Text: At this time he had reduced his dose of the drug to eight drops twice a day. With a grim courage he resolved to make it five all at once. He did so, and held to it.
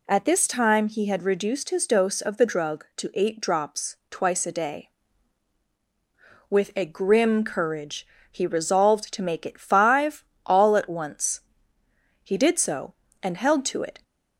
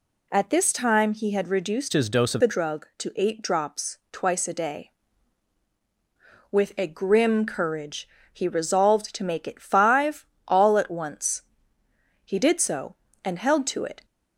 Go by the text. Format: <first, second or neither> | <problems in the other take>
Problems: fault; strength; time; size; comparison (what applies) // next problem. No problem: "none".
first | changes voice from "his" to "of"; from 1.9 to 2.4 s; 0.5 s long // pauses between "courage" and "he"; slight; at 8.0 s; 0.26 s long; slight in the first // pauses between "five" and "all"; slight; at 10.2 s; 0.20 s long; slight in the first